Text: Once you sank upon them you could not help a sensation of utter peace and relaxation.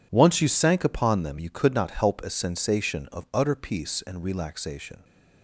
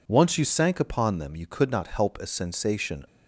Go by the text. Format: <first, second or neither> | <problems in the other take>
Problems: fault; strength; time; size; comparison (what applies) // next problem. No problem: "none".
first | stops before "of utter peace and relaxation"; at 3.0 s